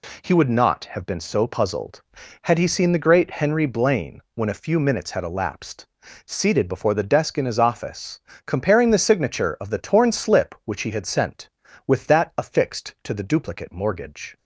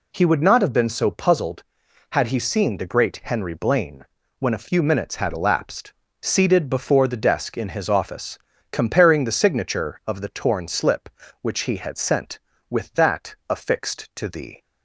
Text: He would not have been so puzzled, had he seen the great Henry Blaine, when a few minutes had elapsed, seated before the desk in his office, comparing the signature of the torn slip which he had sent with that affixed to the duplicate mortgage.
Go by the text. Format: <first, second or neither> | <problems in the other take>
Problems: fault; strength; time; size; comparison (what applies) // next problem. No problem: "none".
first | stops before "duplicate mortgage"; at 14.6 s